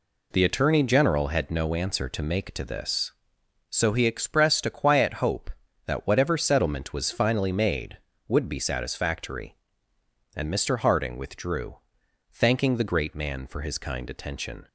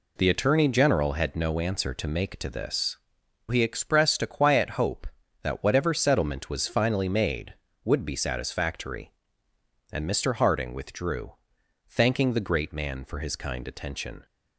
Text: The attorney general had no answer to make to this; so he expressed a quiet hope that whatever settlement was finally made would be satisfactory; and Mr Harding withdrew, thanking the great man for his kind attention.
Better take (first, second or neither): first